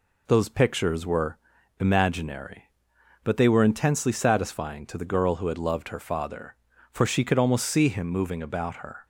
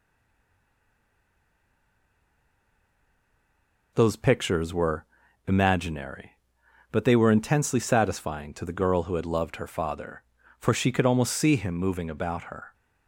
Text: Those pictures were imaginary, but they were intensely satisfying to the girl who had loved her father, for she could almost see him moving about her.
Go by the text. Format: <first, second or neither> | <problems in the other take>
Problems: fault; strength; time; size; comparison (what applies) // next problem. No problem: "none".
first | stays silent before the first word; strong; until 3.9 s; 3.9 s long // pauses between "were" and "imaginary"; at 5.0 s; 0.42 s long; also in the first